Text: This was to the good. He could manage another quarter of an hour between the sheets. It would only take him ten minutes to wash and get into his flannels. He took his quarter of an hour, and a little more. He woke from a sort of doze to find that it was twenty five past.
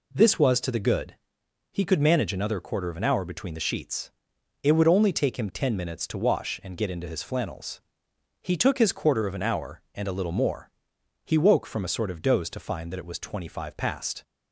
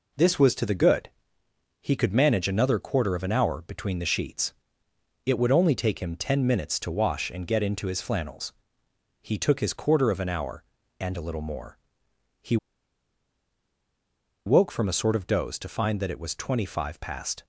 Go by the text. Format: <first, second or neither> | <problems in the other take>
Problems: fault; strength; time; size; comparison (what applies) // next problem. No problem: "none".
first | pauses between "He" and "woke"; strong; at 12.5 s; 1.8 s long